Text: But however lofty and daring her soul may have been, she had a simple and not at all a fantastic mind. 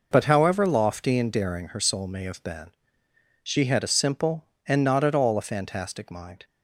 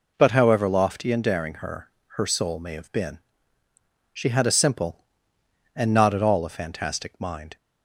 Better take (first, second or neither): first